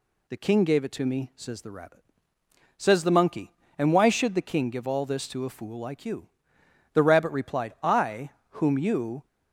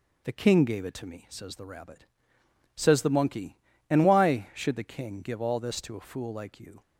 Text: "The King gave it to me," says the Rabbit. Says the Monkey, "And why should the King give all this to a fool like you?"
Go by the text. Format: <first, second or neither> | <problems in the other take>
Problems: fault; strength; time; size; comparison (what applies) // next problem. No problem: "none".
second | goes on to say "The Rabbit replied I whom you"; strong; from 6.9 s on; 2.3 s long